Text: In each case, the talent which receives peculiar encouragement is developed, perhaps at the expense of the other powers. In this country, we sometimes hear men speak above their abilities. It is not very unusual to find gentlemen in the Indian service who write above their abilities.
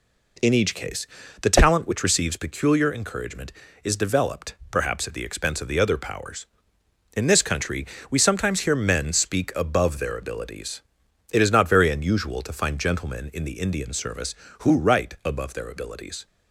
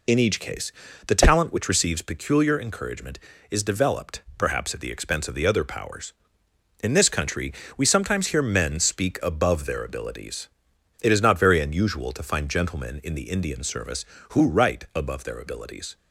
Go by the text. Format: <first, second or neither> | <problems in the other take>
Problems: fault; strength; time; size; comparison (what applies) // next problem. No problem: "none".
first | loses the start of "In"; at 0.0 s; 50 ms